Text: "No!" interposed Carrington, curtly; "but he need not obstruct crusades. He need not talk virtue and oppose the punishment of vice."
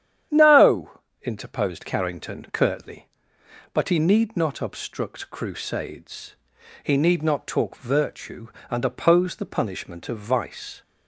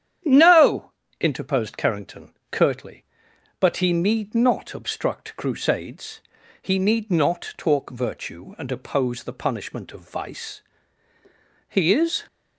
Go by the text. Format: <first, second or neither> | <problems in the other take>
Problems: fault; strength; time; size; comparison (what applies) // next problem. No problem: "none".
first | starts louder than the rest; strong; until 1.5 s; 9.5 dB; strong in the first // goes on to say "He is"; from 11.6 s on; 0.54 s long